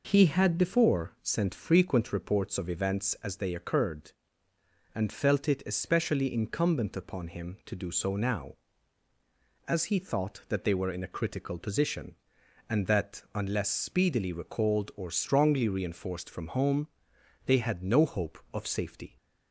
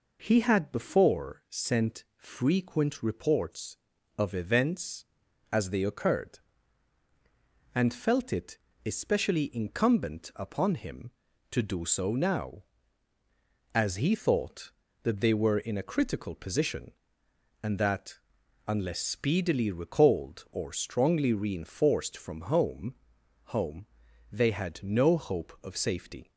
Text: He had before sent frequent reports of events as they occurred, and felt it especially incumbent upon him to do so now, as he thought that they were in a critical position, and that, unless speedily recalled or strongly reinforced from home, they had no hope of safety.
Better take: first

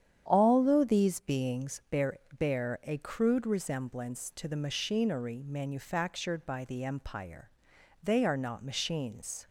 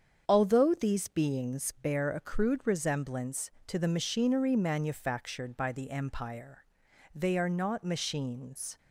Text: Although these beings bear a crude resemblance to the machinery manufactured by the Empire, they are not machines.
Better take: second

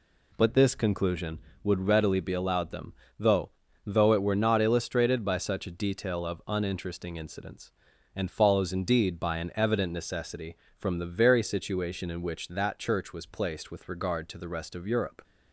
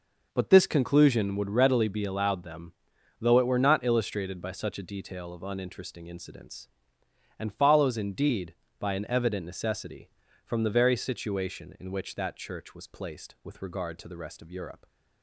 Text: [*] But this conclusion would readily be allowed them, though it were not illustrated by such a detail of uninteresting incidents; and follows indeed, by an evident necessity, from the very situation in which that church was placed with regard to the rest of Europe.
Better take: second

